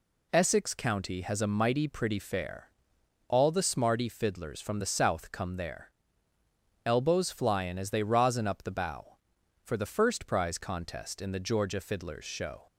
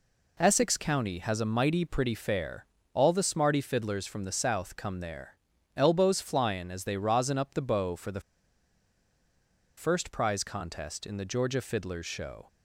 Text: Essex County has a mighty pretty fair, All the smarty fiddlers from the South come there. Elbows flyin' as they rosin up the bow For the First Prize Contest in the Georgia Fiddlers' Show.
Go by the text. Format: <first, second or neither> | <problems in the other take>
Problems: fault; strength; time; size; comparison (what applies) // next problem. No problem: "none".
first | pauses between "the" and "First"; strong; at 8.2 s; 1.5 s long